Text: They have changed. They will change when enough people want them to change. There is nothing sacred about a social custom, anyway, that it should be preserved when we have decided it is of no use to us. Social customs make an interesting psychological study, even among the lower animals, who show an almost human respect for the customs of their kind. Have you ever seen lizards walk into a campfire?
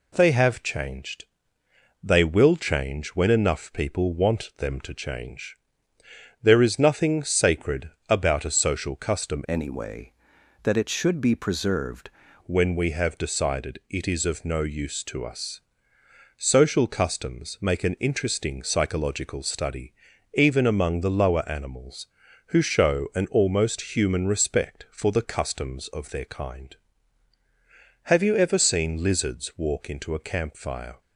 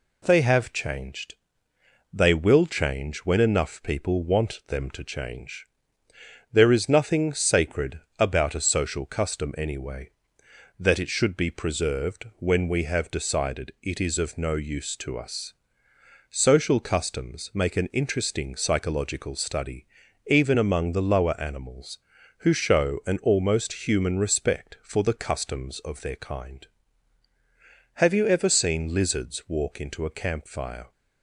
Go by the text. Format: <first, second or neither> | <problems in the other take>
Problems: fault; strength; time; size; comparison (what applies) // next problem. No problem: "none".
second | pauses between "sacred" and "about"; slight; at 7.8 s; 0.20 s long; slight in the second // changes voice from "anyway" to "preserved"; from 9.4 to 12.0 s; 2.6 s long